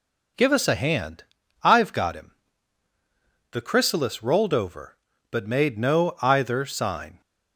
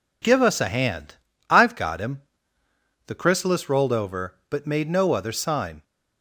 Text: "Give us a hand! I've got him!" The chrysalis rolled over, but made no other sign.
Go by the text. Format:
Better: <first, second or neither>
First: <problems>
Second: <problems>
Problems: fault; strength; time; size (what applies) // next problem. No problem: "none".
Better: second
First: says "either" for "other"; at 6.2 s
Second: none